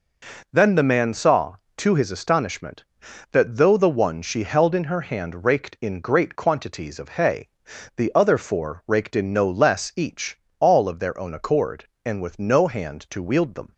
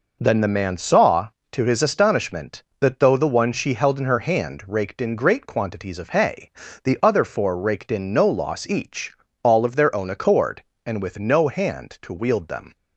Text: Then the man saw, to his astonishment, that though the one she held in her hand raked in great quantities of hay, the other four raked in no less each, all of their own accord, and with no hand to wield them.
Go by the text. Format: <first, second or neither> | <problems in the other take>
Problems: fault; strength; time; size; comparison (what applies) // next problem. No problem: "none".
first | says "loss" for "less"; at 8.2 s